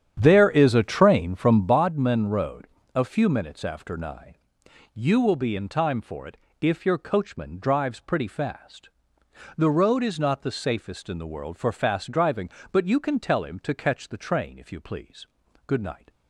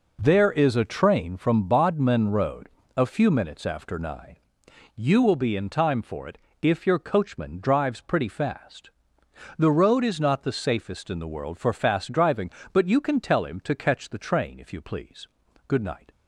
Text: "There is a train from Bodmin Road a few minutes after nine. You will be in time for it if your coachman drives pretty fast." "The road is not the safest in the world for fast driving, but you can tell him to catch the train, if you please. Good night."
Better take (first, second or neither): second